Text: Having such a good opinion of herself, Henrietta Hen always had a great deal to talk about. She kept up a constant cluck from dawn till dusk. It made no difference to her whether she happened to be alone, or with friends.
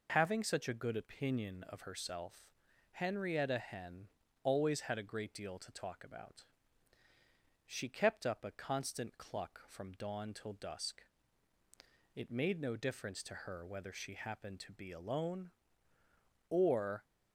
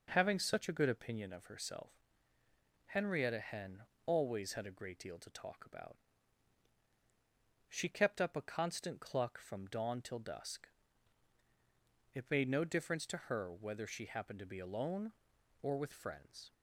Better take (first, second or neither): second